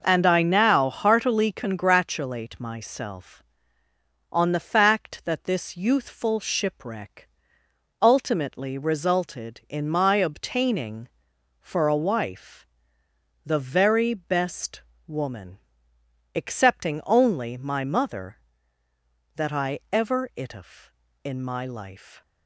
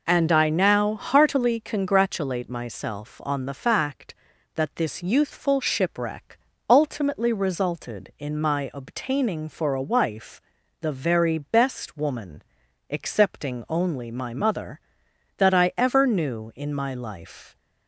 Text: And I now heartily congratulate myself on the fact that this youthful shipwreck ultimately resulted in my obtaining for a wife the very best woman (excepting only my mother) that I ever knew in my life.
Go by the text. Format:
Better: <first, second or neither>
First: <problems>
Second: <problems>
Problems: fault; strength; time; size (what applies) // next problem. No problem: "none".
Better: second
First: pauses between "shipwreck" and "ultimately"; noticeable; at 7.2 s; 0.74 s long // pauses between "wife" and "the"; noticeable; at 12.6 s; 0.80 s long // pauses between "best" and "woman"; slight; at 14.8 s; 0.24 s long // says "itif" for "knew"; at 20.3 s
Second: pauses between "shipwreck" and "ultimately"; slight; at 6.3 s; 0.30 s long // pauses between "wife" and "the"; at 10.4 s; 0.40 s long